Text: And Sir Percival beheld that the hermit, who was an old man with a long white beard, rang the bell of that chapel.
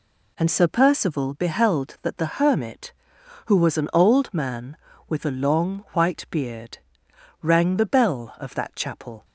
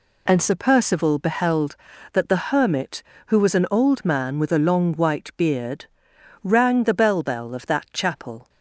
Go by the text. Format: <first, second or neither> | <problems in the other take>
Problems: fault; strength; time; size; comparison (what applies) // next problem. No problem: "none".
first | says "bell" twice; at 7.2 s